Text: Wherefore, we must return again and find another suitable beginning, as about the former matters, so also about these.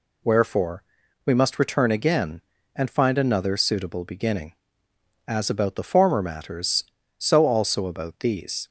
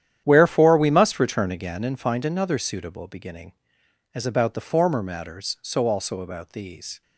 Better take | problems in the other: first | gets quieter; strong; throughout; 14 dB

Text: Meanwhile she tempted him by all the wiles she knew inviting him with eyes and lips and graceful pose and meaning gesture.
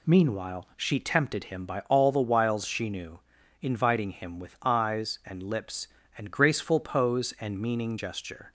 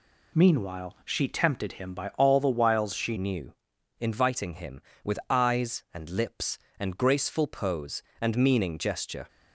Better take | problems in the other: first | changes voice at "knew"; from 3.1 s on; 6.1 s long // pauses between "knew" and "inviting"; noticeable; at 3.5 s; 0.46 s long; also in the first

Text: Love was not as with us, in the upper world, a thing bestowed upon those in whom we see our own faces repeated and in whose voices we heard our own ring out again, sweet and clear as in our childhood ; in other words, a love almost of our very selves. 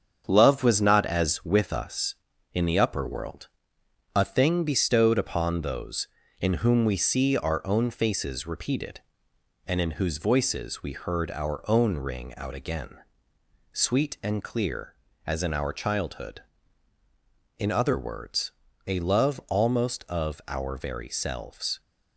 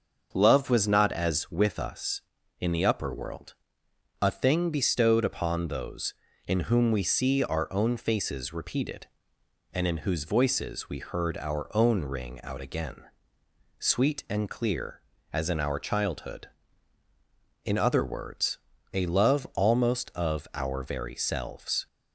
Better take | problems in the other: second | gets quieter; noticeable; throughout; 5.5 dB // starts louder than the rest; strong; until 1.2 s; 7.5 dB; also in the second

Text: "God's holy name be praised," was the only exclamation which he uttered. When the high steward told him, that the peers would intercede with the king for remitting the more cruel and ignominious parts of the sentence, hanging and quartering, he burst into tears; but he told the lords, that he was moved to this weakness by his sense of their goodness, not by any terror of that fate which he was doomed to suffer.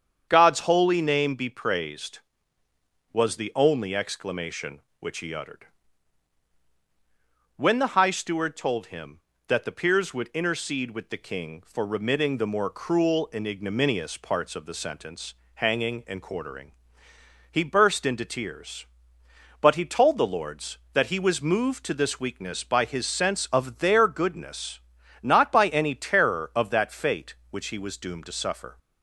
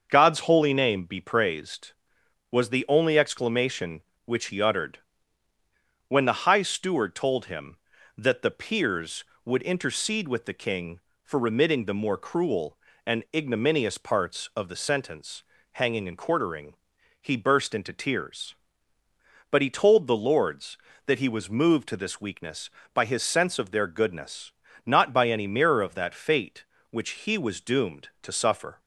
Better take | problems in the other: first | starts louder than the rest; until 1.1 s; 6.5 dB; strong in the first // says "mirror" for "terror"; at 25.4 s

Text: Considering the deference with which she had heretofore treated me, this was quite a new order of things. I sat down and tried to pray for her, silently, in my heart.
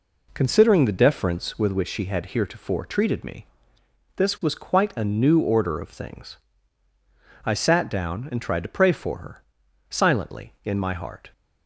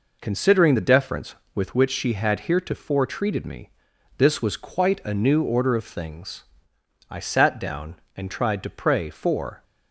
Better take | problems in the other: first | stops before "her silently in my heart"; at 9.6 s

